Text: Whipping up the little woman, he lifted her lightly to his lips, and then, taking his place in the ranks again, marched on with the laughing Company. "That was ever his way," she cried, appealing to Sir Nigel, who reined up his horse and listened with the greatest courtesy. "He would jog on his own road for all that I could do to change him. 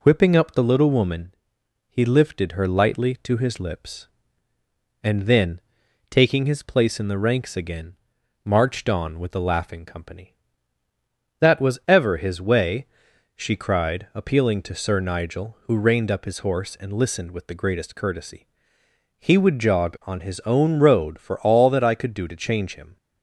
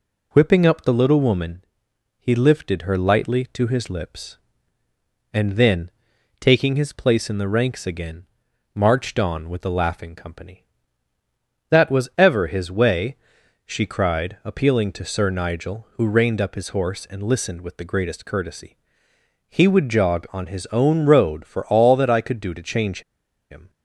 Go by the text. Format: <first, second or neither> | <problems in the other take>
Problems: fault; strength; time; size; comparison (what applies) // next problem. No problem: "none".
first | pauses between "change" and "him"; noticeable; at 23.0 s; 0.49 s long